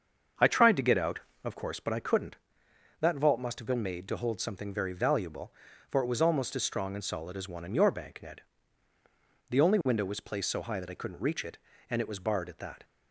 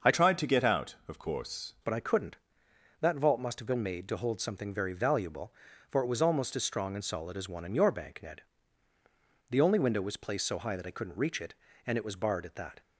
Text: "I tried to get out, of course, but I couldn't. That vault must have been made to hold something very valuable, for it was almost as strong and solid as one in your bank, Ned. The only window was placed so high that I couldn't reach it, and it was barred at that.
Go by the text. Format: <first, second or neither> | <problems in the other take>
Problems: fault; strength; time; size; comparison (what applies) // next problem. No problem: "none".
first | starts louder than the rest; until 1.1 s; 6.5 dB; also in the first // changes voice from "tried" to "course"; from 0.1 to 1.7 s; 1.6 s long